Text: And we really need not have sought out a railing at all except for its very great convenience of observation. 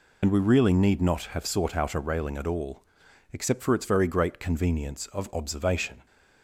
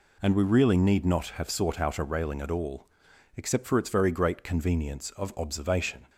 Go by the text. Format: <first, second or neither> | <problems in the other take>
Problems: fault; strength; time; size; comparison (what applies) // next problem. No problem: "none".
second | loses the start of "And"; at 0.2 s; 75 ms // pauses between "all" and "except"; noticeable; at 2.8 s; 0.52 s long; noticeable in the second